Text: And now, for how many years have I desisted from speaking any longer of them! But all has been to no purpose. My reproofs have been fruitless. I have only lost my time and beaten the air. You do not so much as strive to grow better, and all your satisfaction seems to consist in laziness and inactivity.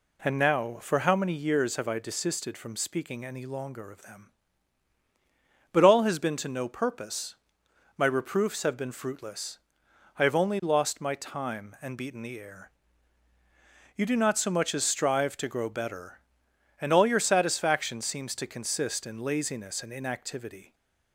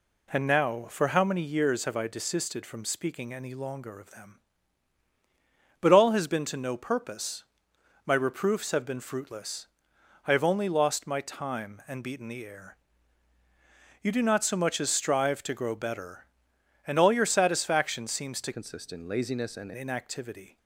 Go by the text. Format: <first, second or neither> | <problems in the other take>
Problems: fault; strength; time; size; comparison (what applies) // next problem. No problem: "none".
first | changes voice from "consist" to "and"; from 18.5 to 19.7 s; 1.2 s long